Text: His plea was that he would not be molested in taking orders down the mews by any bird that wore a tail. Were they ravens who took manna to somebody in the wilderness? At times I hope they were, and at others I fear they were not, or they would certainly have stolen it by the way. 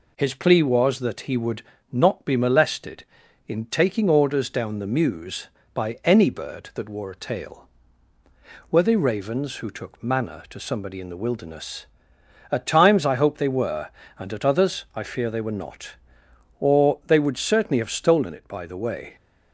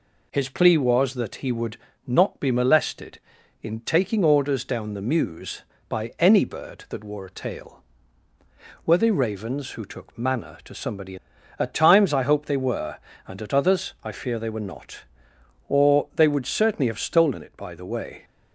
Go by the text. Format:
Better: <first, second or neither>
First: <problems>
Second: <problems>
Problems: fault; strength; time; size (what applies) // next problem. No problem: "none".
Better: first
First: pauses between "would" and "not"; slight; at 1.6 s; 0.28 s long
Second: pauses between "would" and "not"; slight; at 1.7 s; 0.28 s long // skips "in the wilderness"; at 11.3 s